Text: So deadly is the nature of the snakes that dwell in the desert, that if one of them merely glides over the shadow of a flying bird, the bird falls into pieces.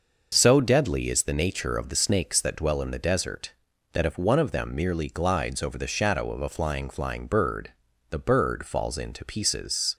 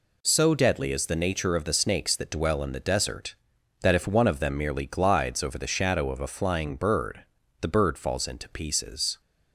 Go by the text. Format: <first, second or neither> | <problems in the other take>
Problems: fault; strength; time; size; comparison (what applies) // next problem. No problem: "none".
second | says "flying" twice; at 6.8 s